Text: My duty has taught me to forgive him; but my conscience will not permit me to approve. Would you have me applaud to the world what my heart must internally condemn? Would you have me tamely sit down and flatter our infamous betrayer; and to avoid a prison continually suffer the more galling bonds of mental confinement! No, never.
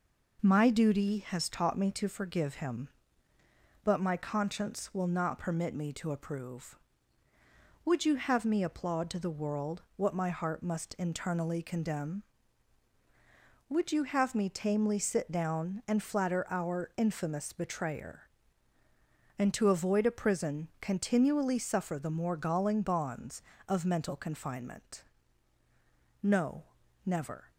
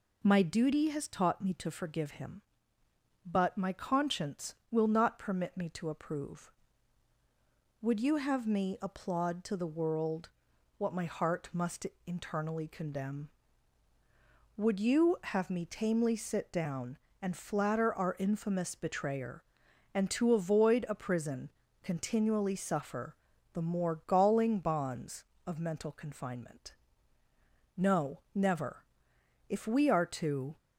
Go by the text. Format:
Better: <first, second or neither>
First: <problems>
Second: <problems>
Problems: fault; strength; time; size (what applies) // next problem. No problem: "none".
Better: first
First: none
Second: pauses between "world" and "what"; noticeable; at 10.2 s; 0.48 s long // pauses between "must" and "internally"; slight; at 11.8 s; 0.18 s long // pauses between "prison" and "continually"; slight; at 21.4 s; 0.32 s long // pauses between "suffer" and "the"; at 23.1 s; 0.38 s long // goes on to say "If we are to"; noticeable; from 29.4 s on; 1.0 s long